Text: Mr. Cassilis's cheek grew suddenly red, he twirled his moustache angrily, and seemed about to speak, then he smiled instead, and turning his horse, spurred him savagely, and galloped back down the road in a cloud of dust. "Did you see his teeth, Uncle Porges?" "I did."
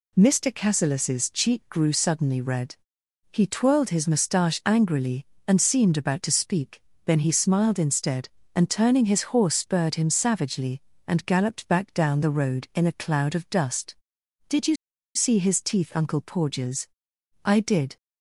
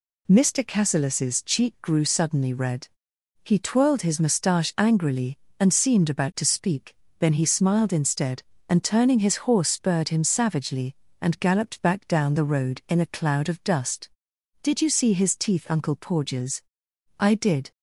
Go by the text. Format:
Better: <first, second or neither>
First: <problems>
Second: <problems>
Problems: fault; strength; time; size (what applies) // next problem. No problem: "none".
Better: second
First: pauses between "you" and "see"; at 14.7 s; 0.40 s long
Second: none